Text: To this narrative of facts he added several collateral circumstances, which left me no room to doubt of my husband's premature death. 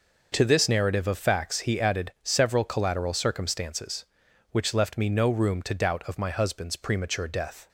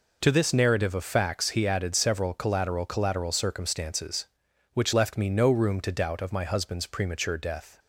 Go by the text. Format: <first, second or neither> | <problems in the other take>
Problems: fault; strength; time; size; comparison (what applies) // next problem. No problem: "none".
first | says "collateral" twice; at 2.8 s